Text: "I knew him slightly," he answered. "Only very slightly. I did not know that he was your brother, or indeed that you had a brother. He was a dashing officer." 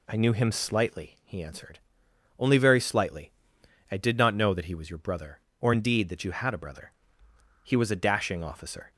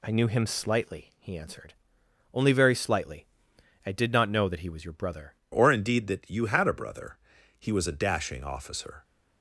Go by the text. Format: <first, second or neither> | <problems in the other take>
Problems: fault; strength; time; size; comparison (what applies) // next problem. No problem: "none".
first | changes voice at "or"; from 5.5 s on; 3.5 s long